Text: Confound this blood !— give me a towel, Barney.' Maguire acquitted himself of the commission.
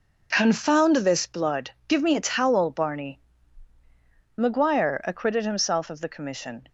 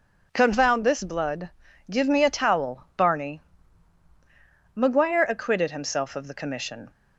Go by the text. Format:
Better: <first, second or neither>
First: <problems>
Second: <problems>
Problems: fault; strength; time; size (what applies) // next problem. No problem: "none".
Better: neither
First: none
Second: none